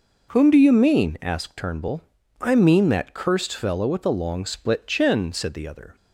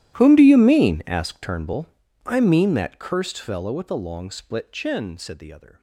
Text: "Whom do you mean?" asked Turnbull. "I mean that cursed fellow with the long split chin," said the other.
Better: first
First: none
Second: gets quieter; strong; throughout; 22.5 dB

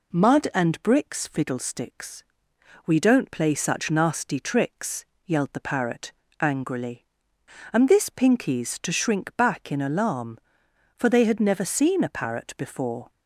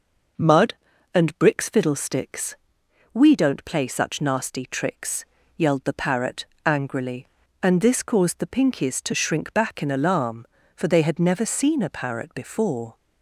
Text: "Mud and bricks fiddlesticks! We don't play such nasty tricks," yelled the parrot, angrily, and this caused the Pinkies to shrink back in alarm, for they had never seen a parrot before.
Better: second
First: skips "caused the"; at 8.0 s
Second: none

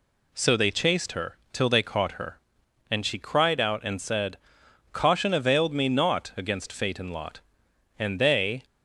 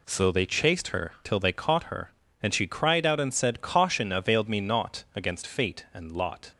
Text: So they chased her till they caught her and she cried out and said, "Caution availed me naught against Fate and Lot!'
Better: second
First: pauses between "her" and "till"; slight; at 1.3 s; 0.16 s long // goes on to say "and they"; noticeable; from 7.9 s on; 0.66 s long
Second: none

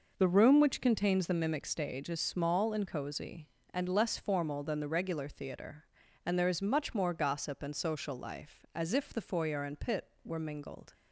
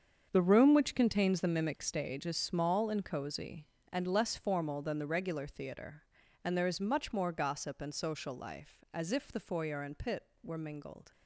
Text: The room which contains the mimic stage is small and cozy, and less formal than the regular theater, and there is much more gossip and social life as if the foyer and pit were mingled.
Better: first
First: none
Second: gets quieter; strong; throughout; 12.5 dB

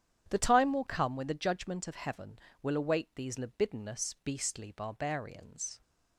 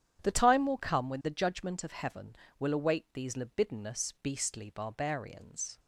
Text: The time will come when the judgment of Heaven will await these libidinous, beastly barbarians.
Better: neither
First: starts louder than the rest; strong; until 1.2 s; 9.5 dB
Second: starts louder than the rest; strong; until 1.2 s; 9.5 dB

